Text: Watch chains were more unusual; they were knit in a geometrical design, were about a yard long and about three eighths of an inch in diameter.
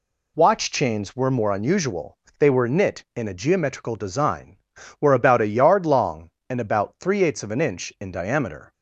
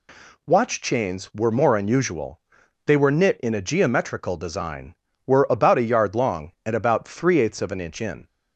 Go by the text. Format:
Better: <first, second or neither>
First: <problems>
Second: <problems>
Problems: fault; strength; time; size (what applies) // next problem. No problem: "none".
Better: first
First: none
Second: stops before "diameter"; at 8.2 s